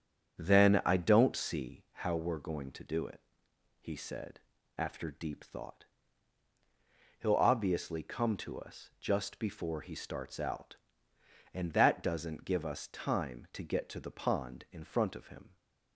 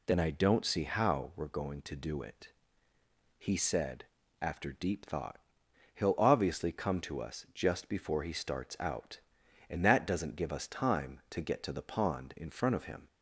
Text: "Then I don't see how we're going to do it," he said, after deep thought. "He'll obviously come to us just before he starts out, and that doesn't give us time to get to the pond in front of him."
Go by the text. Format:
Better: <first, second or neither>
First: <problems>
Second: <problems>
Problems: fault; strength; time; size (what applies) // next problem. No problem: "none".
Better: second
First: starts louder than the rest; strong; until 1.8 s; 8 dB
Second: none